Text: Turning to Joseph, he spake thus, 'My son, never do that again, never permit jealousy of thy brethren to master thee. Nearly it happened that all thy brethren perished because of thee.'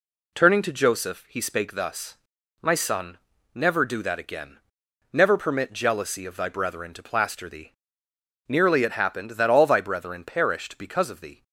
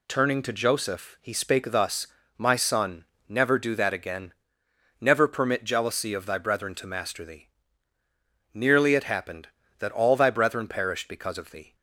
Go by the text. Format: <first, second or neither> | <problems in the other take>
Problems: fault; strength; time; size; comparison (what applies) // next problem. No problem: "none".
second | says "plaster" for "master"; at 7.0 s